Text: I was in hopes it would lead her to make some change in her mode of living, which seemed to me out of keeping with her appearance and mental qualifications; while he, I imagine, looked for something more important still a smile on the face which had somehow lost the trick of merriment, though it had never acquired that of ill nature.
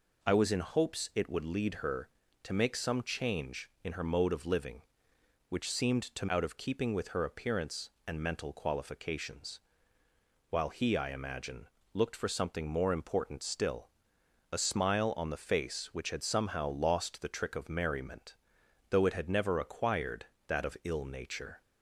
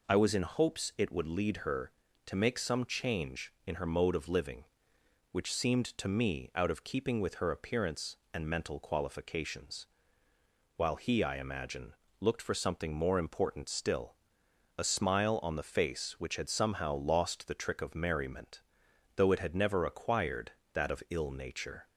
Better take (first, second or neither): second